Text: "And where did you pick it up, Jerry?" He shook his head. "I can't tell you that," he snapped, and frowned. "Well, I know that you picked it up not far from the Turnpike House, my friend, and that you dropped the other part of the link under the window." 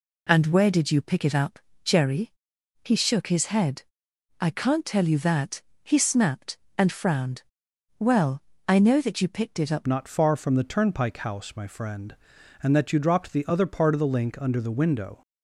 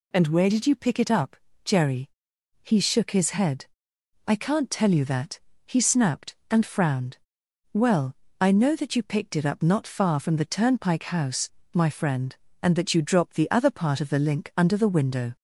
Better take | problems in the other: second | changes voice at "not"; from 9.8 s on; 5.4 s long

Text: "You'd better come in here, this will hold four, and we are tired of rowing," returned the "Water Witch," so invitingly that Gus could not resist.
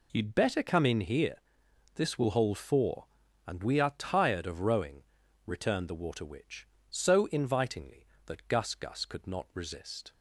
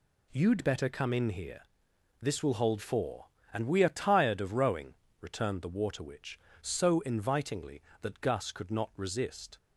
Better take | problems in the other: second | says "Gus" twice; at 8.7 s

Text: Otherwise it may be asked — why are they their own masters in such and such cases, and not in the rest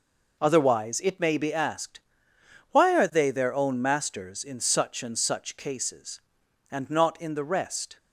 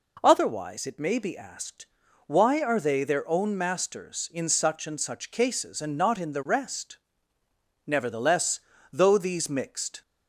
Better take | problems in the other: first | goes on to say "Nevertheless though these mixed"; strong; from 7.8 s on; 2.1 s long

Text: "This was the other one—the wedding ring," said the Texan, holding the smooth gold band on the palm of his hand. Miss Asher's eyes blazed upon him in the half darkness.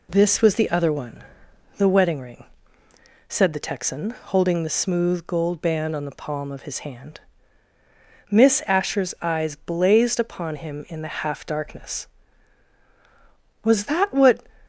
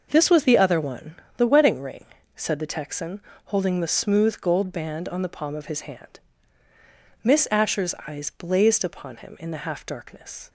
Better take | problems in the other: second | goes on to say "Was that what"; noticeable; from 13.6 s on; 0.78 s long

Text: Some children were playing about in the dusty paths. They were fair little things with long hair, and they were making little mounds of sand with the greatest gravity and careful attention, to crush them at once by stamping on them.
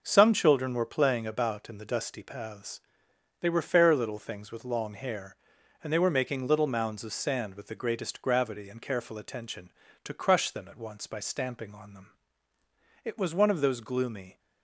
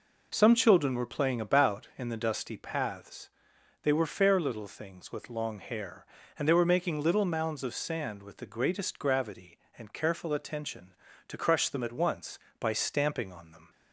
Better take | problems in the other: second | goes on to say "It was one of those gloomy"; from 13.0 s on; 1.3 s long

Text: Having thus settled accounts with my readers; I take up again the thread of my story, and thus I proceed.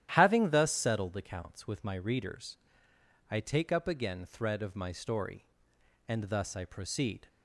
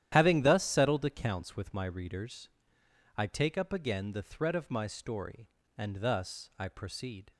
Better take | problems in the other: second | starts louder than the rest; strong; until 1.1 s; 11.5 dB; strong in the second // skips "the"; at 4.2 s

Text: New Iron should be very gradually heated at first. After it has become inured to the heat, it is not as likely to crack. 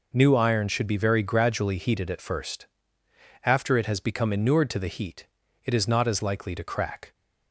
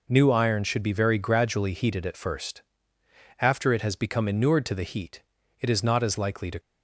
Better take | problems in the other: first | stops before "crack"; at 6.5 s

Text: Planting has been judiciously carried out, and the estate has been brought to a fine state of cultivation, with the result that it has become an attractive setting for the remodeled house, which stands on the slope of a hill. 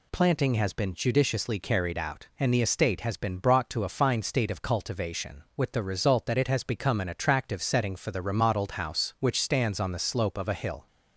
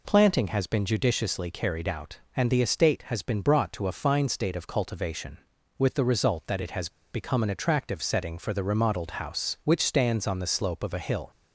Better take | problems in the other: first | pauses between "has" and "become"; slight; at 6.8 s; 0.23 s long

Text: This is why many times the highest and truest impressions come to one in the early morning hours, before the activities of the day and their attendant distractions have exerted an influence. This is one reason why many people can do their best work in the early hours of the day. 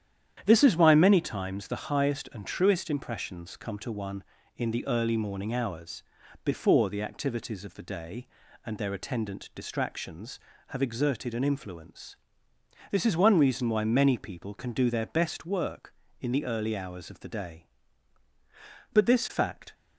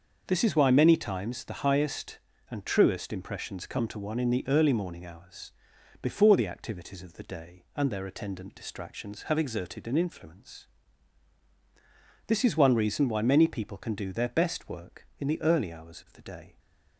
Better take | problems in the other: second | starts louder than the rest; strong; until 1.4 s; 10 dB; also in the second // goes on to say "But this fact"; noticeable; from 18.9 s on; 0.81 s long

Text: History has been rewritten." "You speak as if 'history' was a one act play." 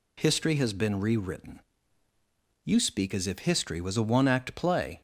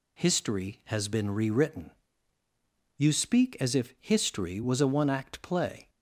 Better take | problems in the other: neither | none

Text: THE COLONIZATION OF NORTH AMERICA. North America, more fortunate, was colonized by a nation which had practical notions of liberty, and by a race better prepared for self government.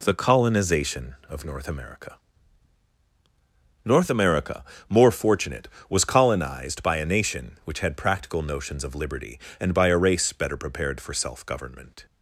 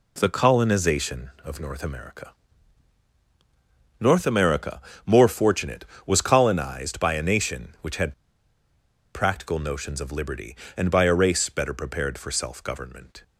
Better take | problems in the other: first | pauses between "had" and "practical"; at 8.1 s; 1.0 s long

